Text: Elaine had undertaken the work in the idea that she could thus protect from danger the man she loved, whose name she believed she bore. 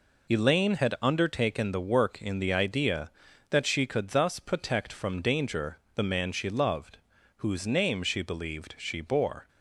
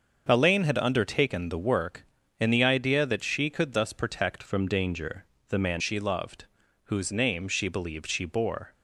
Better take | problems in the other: first | starts louder than the rest; until 1.3 s; 6.5 dB // changes voice from "from" to "man"; from 4.4 to 5.8 s; 1.4 s long // pauses between "danger" and "the"; slight; at 5.2 s; 0.24 s long; slight in the first

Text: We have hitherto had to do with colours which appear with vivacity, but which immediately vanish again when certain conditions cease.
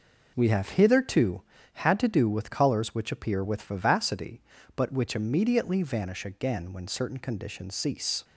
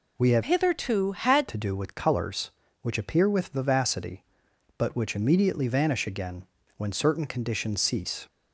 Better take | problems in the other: first | changes voice from "hitherto" to "had"; from 0.4 to 1.4 s; 1.0 s long // pauses between "again" and "when"; slight; at 6.4 s; 0.32 s long

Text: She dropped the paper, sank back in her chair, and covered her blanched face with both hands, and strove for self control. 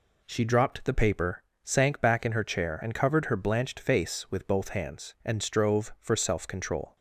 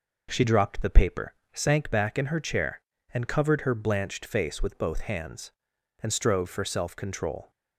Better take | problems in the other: neither | none

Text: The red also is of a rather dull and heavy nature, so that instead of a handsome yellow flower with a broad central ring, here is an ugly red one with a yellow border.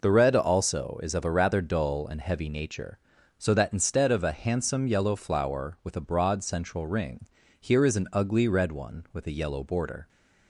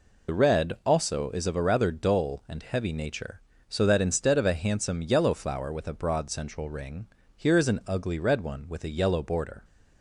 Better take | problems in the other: first | loses the start of "The"; at 0.2 s; 45 ms

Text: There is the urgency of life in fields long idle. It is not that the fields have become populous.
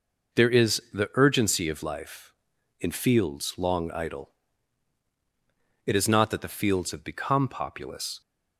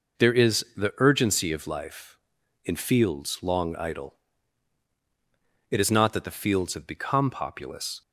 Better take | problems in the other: neither | none

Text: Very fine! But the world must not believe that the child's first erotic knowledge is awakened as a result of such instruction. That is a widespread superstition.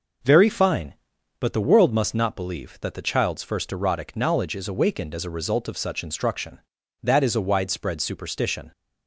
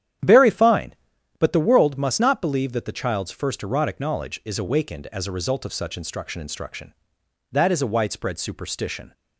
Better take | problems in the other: first | starts louder than the rest; strong; until 1.6 s; 10 dB // says "instruction" twice; at 6.4 s

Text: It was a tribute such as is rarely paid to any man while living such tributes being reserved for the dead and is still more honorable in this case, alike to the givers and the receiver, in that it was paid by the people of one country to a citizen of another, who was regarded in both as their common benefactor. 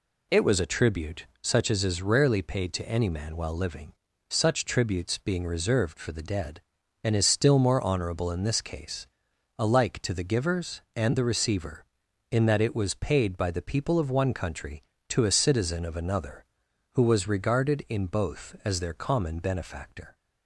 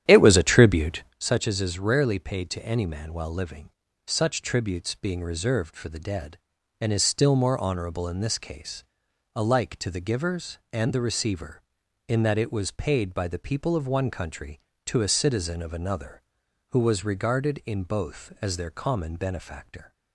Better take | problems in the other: first | starts louder than the rest; strong; until 1.2 s; 10.5 dB // pauses between "tribute" and "such"; slight; at 1.0 s; 0.16 s long; slight in the first // pauses between "living" and "such"; slight; at 3.6 s; 0.36 s long; slight in the first

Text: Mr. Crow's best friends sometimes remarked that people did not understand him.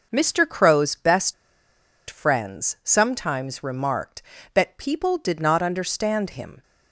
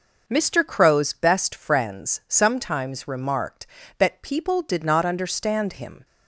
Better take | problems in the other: second | pauses between "best" and "friends"; noticeable; at 1.3 s; 0.75 s long

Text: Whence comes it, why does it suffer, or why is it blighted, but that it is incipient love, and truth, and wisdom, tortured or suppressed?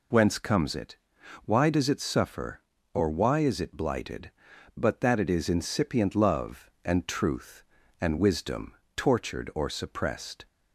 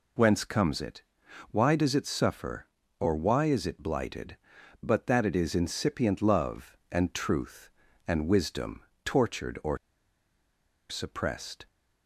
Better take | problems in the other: first | pauses between "or" and "suppressed"; at 9.7 s; 1.1 s long

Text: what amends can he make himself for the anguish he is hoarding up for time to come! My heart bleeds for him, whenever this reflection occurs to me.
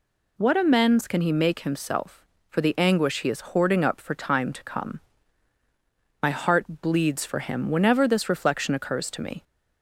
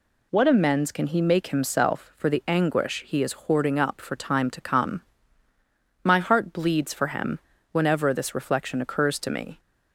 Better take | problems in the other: neither | none

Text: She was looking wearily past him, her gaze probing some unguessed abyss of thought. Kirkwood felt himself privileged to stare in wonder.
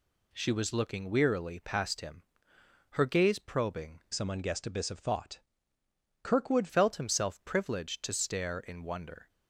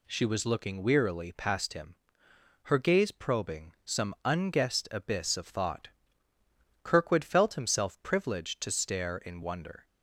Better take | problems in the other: second | changes voice from "some" to "Kirkwood"; from 4.1 to 6.6 s; 2.5 s long

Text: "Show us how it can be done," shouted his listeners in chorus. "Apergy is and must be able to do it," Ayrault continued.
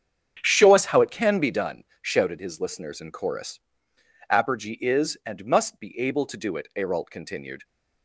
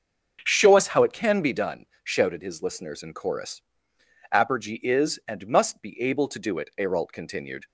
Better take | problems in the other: second | gets quieter; strong; throughout; 11.5 dB // starts louder than the rest; strong; until 1.4 s; 8 dB; also in the second

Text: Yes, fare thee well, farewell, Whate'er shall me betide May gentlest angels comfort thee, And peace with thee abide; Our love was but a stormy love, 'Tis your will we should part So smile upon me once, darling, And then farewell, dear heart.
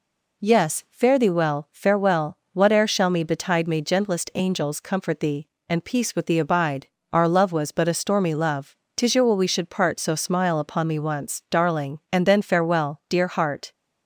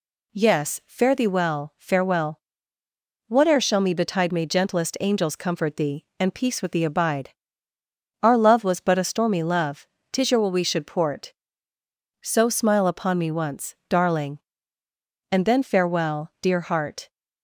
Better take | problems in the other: first | says "port" for "part"; at 10.8 s

